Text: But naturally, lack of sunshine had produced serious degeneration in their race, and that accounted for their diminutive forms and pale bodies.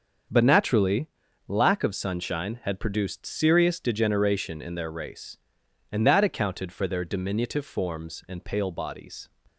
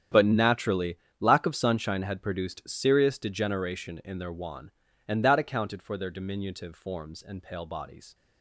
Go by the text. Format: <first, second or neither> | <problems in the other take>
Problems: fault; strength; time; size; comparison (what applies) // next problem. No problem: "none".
first | starts louder than the rest; strong; until 1.3 s; 9 dB; also in the first // says "wan" for "race"; at 4.3 s